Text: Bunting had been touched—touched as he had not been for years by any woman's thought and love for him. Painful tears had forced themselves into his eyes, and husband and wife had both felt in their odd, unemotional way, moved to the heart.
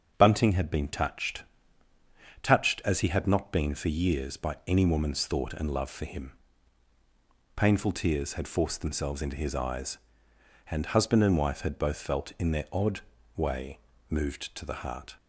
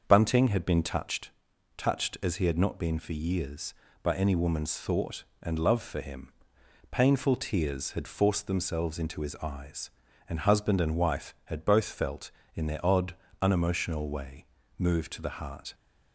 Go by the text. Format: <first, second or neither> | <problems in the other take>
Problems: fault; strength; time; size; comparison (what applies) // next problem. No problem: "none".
second | starts louder than the rest; until 1.1 s; 6.5 dB; also in the second // skips "unemotional"; at 13.1 s